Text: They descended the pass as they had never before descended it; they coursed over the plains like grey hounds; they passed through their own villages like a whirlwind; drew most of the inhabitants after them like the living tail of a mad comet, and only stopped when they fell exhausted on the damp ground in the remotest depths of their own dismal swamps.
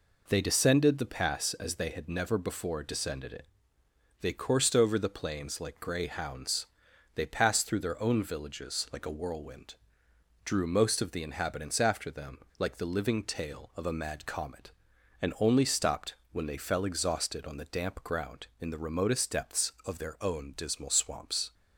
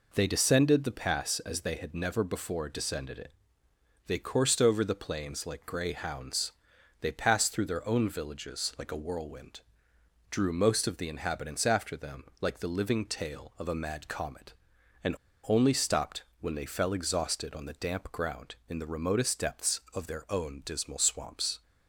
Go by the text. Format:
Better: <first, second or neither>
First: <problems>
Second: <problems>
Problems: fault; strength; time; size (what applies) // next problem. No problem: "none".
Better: first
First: pauses between "them" and "like"; slight; at 12.3 s; 0.19 s long // pauses between "stopped" and "when"; slight; at 16.1 s; 0.18 s long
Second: pauses between "them" and "like"; slight; at 12.2 s; 0.16 s long // pauses between "and" and "only"; slight; at 15.1 s; 0.32 s long // pauses between "stopped" and "when"; slight; at 16.2 s; 0.18 s long